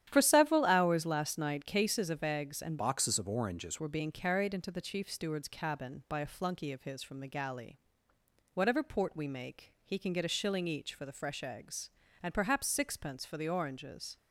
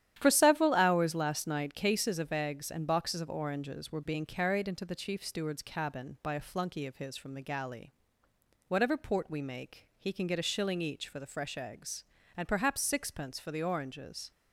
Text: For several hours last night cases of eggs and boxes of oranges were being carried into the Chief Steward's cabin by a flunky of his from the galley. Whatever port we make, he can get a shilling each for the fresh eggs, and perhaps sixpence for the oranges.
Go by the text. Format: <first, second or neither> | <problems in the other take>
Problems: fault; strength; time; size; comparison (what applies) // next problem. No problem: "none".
second | starts louder than the rest; strong; until 1.1 s; 10.5 dB; strong in the second // changes voice from "boxes" to "oranges"; from 2.7 to 3.7 s; 1.0 s long